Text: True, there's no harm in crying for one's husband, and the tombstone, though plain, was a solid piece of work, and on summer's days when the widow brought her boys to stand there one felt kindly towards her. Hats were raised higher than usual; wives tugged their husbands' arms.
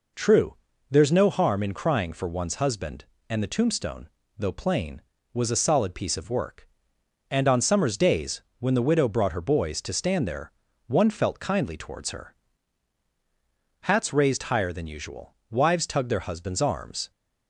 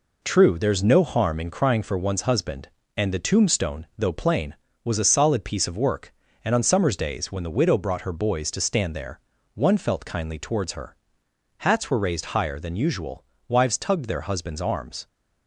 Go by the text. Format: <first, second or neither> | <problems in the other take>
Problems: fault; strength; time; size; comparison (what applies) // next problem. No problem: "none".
second | pauses between "days" and "when"; slight; at 8.4 s; 0.16 s long // pauses between "there" and "one"; slight; at 10.5 s; 0.34 s long; slight in the second // skips "were"; at 14.1 s